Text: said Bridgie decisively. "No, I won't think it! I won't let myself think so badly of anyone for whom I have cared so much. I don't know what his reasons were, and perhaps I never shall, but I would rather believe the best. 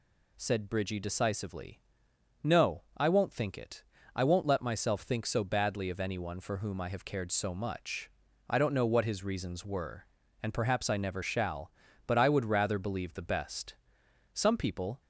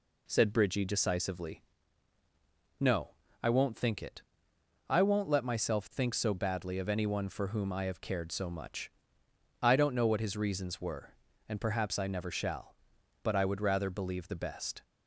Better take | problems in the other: second | goes on to say "Some people"; noticeable; from 14.3 s on; 0.68 s long

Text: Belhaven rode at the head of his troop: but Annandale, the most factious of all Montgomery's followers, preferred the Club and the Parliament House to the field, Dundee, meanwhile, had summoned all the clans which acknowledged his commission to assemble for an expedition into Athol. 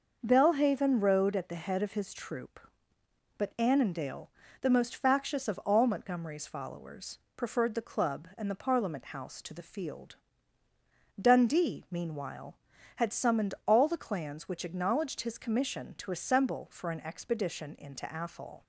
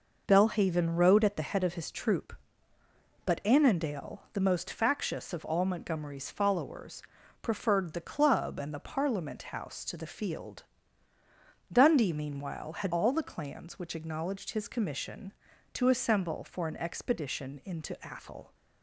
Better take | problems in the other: first | skips "summoned"; at 12.9 s

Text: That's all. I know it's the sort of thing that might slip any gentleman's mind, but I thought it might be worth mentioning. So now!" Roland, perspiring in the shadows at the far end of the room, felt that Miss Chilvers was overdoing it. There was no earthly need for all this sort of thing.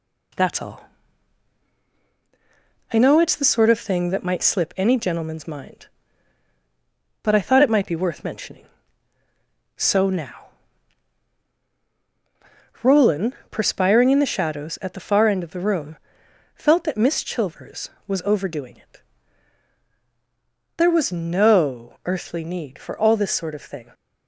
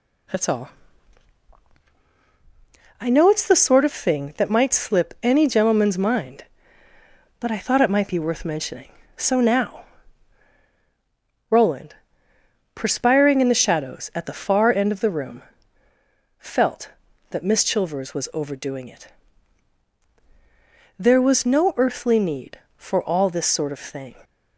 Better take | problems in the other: neither | none

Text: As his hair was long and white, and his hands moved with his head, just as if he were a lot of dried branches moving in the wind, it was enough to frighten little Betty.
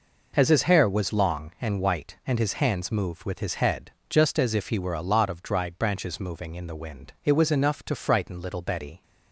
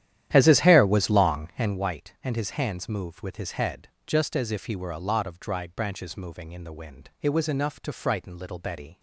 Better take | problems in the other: first | starts louder than the rest; strong; until 1.8 s; 11.5 dB

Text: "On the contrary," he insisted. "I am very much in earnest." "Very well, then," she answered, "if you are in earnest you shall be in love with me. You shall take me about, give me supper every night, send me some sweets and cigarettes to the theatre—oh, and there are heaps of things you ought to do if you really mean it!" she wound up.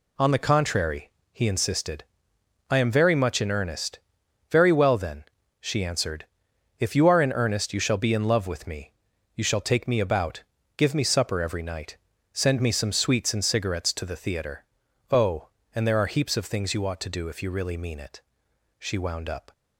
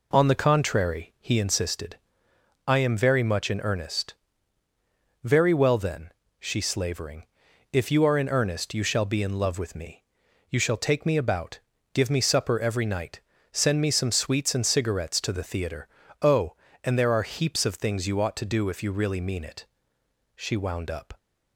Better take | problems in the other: first | says "slavering" for "answered"; at 6.5 s

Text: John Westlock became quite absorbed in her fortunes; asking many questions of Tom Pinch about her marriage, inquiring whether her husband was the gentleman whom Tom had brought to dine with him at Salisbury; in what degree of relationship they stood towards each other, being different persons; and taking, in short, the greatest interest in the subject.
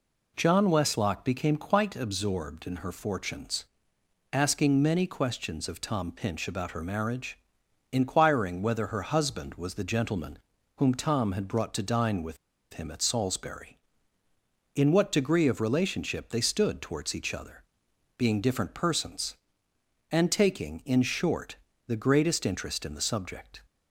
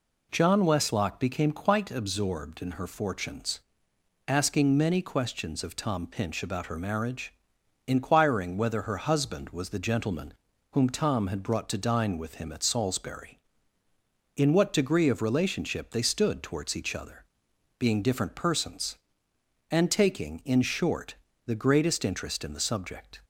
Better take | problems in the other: second | pauses between "gentleman" and "whom"; at 10.3 s; 0.38 s long; also in the second // pauses between "with" and "him"; at 12.3 s; 0.36 s long

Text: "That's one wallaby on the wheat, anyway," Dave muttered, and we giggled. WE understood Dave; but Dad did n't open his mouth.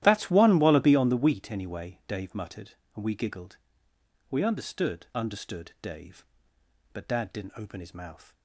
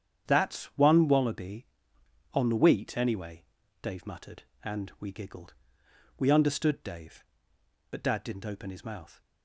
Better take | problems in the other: second | starts louder than the rest; strong; until 1.0 s; 13 dB; strong in the second // says "understood" twice; at 5.1 s

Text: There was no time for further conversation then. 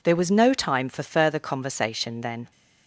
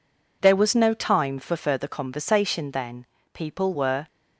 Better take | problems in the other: first | goes on to say "People were"; noticeable; from 3.3 s on; 0.72 s long

